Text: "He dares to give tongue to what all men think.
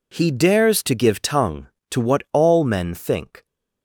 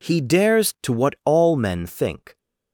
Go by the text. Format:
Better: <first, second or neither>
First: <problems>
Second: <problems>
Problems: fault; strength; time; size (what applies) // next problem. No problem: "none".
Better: first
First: none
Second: skips "to give tongue"; at 0.7 s